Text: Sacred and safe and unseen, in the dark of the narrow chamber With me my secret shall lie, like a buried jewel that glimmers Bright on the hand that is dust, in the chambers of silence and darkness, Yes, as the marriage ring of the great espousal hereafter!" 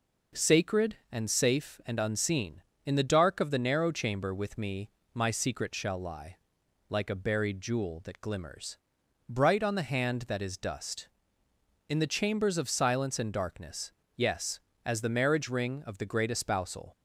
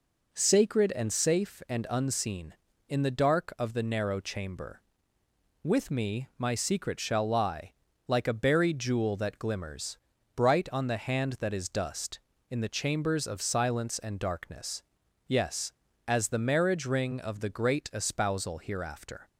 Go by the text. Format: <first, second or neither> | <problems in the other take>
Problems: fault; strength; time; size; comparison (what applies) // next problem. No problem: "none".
second | pauses between "me" and "my"; slight; at 4.8 s; 0.24 s long // pauses between "glimmers" and "Bright"; noticeable; at 8.7 s; 0.54 s long; also in the second // stops before "hereafter"; at 16.9 s